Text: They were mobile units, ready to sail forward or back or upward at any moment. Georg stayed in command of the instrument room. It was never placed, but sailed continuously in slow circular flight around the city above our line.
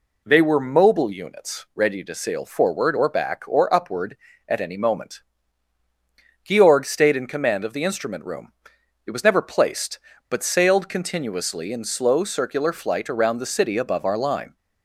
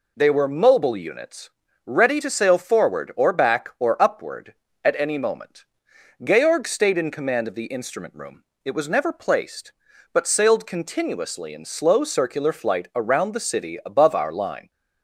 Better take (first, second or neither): neither